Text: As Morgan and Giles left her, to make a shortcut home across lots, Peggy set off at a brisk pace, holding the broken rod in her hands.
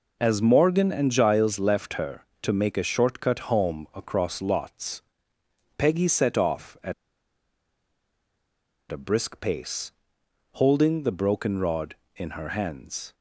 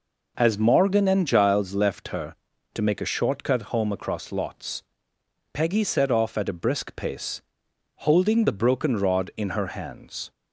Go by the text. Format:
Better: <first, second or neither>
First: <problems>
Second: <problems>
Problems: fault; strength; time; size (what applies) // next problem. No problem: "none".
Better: second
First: pauses between "at" and "a"; strong; at 6.9 s; 1.9 s long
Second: none